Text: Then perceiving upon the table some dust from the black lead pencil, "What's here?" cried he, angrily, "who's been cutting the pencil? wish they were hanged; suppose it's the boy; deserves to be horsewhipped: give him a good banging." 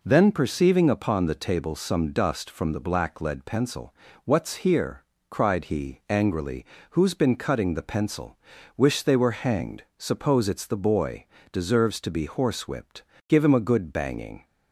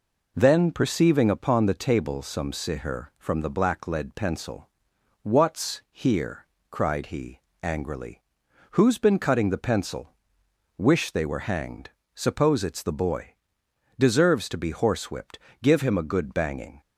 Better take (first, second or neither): first